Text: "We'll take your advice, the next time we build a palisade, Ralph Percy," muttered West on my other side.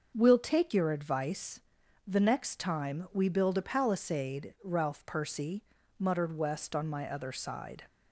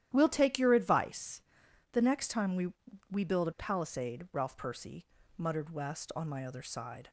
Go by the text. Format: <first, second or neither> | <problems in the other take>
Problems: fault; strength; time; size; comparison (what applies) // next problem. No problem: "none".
first | starts louder than the rest; strong; until 1.1 s; 11.5 dB; also in the first // says "we" twice; at 3.1 s